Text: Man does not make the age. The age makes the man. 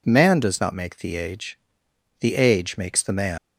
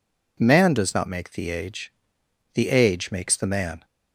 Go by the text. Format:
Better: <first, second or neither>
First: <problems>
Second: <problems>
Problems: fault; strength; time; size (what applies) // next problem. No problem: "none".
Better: second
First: leaves "man" unfinished; at 3.3 s; 125 ms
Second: none